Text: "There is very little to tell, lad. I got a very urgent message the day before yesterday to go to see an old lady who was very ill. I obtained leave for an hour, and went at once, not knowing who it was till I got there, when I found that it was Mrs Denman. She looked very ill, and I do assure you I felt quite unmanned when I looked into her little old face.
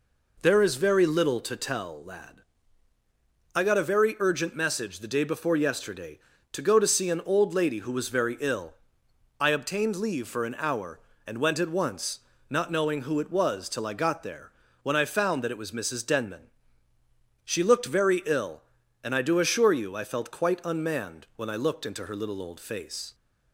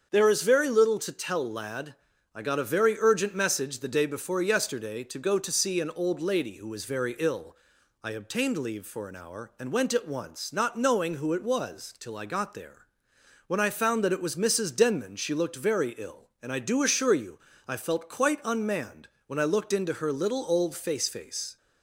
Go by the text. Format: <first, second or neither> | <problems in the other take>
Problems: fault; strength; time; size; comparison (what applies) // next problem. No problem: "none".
first | starts louder than the rest; until 1.1 s; 7 dB // pauses between "you" and "I"; slight; at 17.4 s; 0.26 s long // pauses between "unmanned" and "when"; slight; at 19.0 s; 0.18 s long // says "face" twice; at 21.0 s